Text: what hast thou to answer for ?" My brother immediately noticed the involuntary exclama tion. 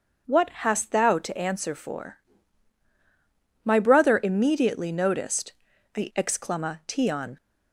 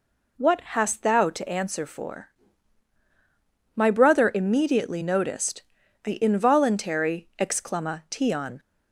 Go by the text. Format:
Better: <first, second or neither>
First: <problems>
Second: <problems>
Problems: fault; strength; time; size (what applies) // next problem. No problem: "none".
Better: second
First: pauses between "noticed" and "the"; at 5.5 s; 0.42 s long // skips "involuntary"; at 6.1 s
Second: pauses between "noticed" and "the"; at 5.6 s; 0.42 s long